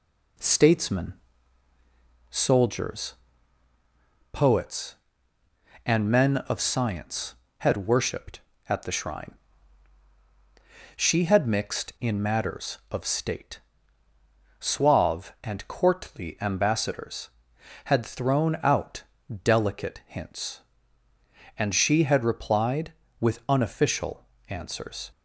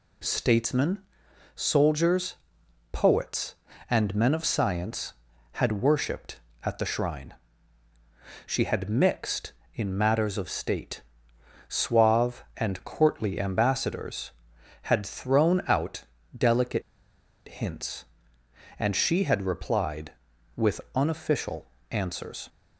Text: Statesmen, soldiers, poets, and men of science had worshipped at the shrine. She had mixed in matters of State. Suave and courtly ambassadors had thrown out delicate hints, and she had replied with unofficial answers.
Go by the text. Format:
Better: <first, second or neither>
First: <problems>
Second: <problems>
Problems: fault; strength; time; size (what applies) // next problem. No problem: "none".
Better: first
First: pauses between "out" and "delicate"; at 19.0 s; 0.40 s long // pauses between "unofficial" and "answers"; slight; at 24.2 s; 0.24 s long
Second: pauses between "out" and "delicate"; slight; at 16.0 s; 0.32 s long // pauses between "delicate" and "hints"; noticeable; at 16.8 s; 0.66 s long // pauses between "unofficial" and "answers"; slight; at 21.6 s; 0.24 s long